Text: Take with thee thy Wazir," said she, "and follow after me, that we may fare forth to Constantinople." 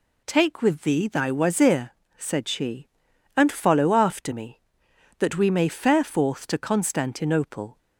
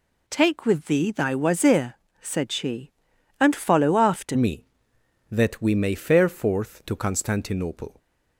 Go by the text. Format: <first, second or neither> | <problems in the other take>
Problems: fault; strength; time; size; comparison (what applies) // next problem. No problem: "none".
first | changes voice at "me"; from 4.3 s on; 3.6 s long